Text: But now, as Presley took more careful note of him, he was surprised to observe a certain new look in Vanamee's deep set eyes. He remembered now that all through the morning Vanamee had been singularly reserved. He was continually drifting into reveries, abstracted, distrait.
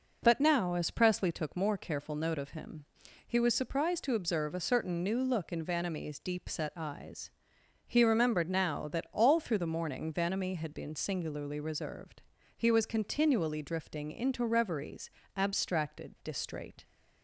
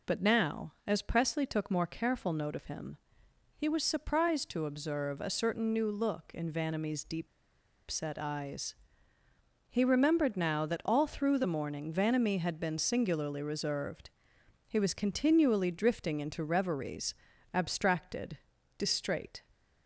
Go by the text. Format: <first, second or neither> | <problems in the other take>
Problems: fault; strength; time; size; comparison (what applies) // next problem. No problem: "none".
first | pauses between "deep" and "set"; noticeable; at 7.2 s; 0.62 s long